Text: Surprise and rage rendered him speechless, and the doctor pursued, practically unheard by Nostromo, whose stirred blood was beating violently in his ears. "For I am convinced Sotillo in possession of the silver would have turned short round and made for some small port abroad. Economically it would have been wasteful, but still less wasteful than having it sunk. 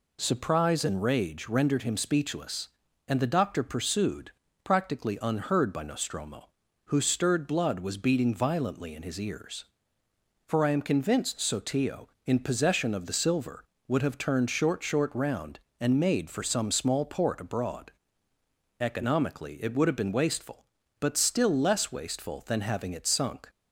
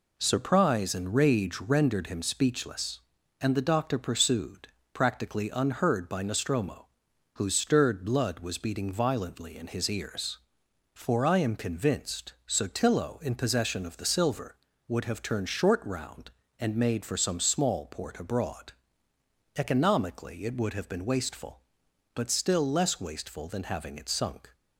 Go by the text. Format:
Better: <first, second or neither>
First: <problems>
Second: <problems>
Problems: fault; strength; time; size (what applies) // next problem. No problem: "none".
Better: second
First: says "short" twice; at 14.8 s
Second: none